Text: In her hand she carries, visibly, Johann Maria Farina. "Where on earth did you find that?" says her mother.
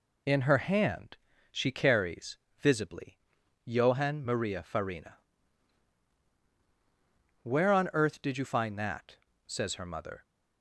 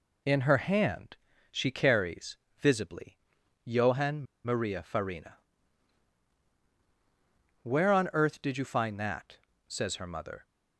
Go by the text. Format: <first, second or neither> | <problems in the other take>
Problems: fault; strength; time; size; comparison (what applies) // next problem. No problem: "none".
first | pauses between "hand" and "she"; slight; at 1.1 s; 0.34 s long; slight in the first // pauses between "Johann" and "Maria"; slight; at 4.2 s; 0.19 s long